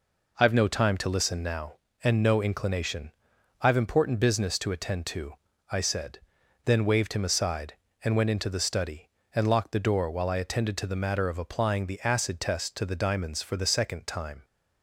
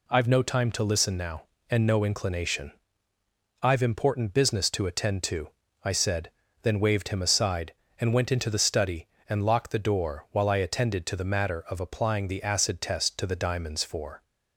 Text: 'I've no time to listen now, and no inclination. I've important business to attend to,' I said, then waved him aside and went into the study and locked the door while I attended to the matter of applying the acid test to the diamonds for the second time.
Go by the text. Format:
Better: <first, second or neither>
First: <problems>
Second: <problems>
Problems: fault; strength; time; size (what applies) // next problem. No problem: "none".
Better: first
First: none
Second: stops before "the second time"; at 14.2 s